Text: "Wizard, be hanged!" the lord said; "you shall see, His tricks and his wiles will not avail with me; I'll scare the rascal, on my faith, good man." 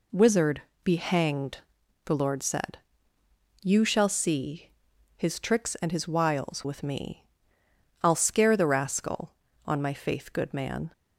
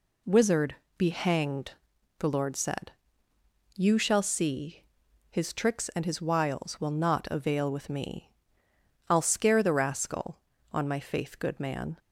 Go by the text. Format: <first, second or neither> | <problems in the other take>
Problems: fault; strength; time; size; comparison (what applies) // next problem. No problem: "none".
second | skips "will not avail"; at 6.6 s